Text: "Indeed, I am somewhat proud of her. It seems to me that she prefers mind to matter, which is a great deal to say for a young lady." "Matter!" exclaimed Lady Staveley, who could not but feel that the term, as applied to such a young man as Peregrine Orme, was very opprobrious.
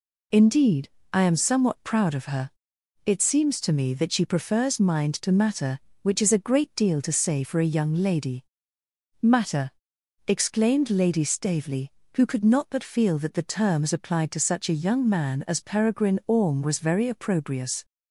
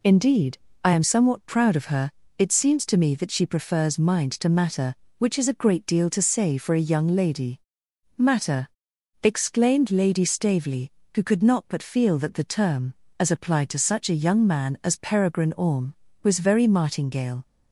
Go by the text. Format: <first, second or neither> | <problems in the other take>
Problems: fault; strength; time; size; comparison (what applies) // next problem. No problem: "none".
first | says "martingale" for "opprobrious"; at 16.6 s